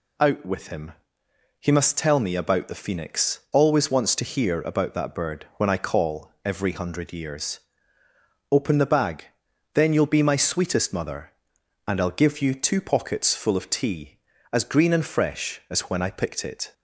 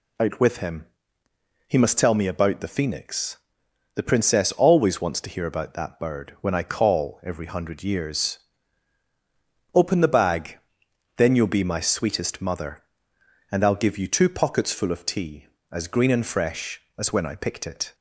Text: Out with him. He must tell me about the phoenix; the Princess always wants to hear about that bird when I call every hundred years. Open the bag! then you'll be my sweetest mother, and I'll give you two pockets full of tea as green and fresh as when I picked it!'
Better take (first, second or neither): second